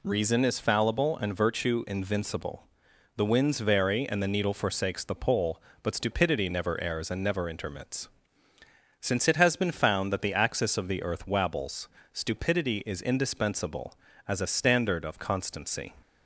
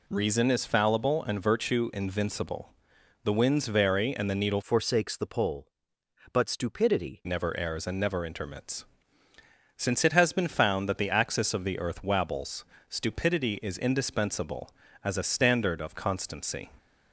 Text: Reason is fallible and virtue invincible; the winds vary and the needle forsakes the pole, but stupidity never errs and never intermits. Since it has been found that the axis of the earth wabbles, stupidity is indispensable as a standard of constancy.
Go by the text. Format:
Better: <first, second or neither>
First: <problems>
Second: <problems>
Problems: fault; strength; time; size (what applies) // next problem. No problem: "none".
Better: first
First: none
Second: changes voice from "forsakes" to "stupidity"; from 4.6 to 7.2 s; 2.6 s long